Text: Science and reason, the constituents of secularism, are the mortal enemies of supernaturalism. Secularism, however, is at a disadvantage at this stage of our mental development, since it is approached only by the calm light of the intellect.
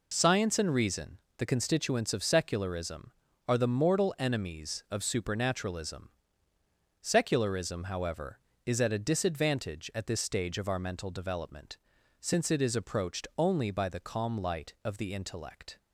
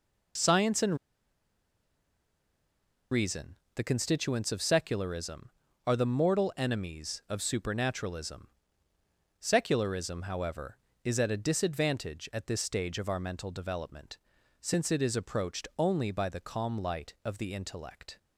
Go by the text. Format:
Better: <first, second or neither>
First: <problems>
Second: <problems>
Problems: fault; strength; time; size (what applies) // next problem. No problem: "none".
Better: first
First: none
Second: pauses between "and" and "reason"; strong; at 0.9 s; 2.1 s long